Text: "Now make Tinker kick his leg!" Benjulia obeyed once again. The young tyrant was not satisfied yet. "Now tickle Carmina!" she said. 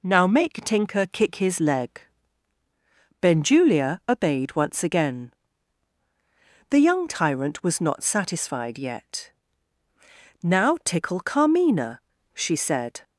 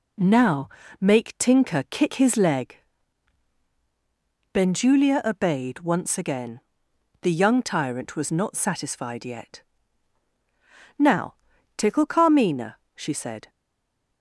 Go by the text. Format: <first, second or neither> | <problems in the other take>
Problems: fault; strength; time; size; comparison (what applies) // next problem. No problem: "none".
first | pauses between "Now" and "make"; slight; at 0.6 s; 0.32 s long // pauses between "Now" and "tickle"; at 11.3 s; 0.42 s long // stays silent after the last word; slight; from 13.4 s on; 0.8 s long